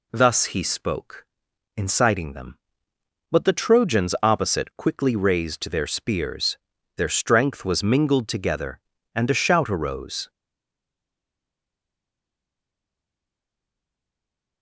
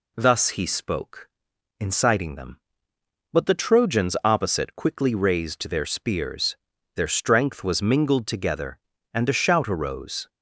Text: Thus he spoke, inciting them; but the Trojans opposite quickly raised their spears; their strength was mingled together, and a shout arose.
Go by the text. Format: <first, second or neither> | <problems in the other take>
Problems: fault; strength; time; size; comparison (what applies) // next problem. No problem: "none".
second | stays silent after the last word; strong; from 10.2 s on; 4.4 s long